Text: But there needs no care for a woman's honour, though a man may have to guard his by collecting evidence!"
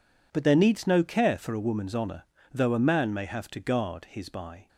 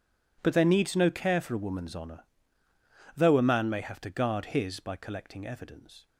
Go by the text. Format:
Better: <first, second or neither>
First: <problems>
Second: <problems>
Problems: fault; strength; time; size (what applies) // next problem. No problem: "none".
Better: second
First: stops before "collecting evidence"; at 4.6 s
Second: none